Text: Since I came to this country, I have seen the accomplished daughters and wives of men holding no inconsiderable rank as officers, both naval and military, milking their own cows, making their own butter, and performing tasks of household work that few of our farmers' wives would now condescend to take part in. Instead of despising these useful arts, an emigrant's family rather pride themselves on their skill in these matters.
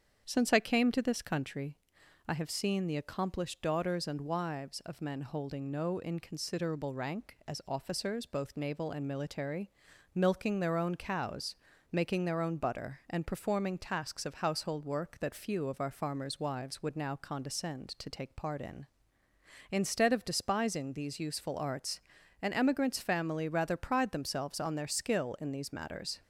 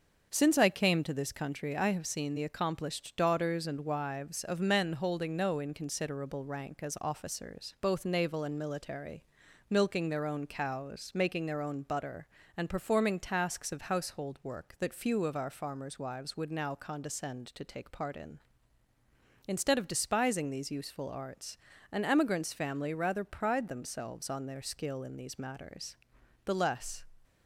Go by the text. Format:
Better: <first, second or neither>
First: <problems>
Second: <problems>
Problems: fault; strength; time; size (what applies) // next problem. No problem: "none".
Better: first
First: starts louder than the rest; strong; until 1.2 s; 7.5 dB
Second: starts louder than the rest; until 1.3 s; 6.5 dB // goes on to say "The less"; from 26.4 s on; 0.58 s long